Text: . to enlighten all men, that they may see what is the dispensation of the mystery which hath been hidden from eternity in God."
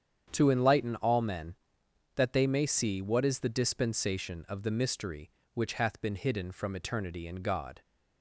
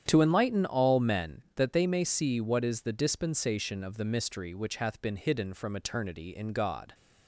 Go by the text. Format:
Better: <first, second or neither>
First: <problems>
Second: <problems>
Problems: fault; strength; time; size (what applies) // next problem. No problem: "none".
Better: neither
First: starts louder than the rest; strong; until 1.3 s; 8.5 dB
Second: starts louder than the rest; strong; until 1.0 s; 9 dB